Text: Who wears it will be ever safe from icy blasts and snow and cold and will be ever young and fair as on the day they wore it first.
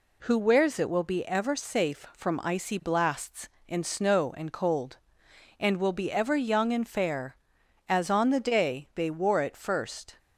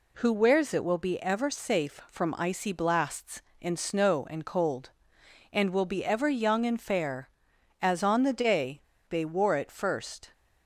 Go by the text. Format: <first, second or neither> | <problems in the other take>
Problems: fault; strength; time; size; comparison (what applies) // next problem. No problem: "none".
first | pauses between "day" and "they"; slight; at 8.7 s; 0.29 s long